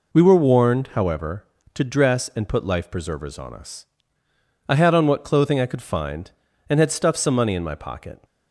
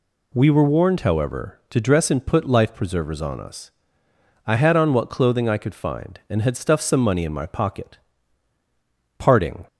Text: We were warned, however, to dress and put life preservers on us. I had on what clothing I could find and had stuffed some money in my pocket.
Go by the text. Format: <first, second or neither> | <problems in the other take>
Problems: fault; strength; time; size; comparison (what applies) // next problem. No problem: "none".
first | goes on to say "PARTING"; slight; from 9.1 s on; 0.48 s long